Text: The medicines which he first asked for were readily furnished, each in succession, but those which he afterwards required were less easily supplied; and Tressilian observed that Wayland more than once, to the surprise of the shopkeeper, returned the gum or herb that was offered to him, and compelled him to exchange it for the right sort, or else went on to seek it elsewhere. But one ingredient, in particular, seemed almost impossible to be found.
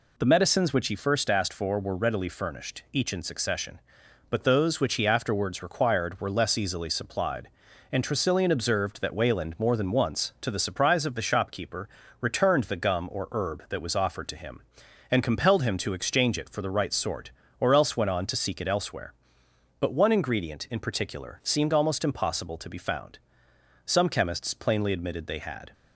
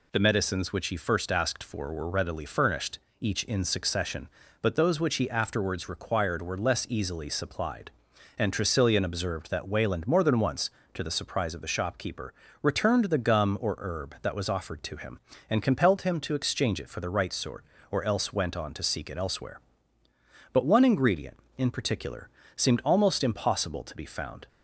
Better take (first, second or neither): second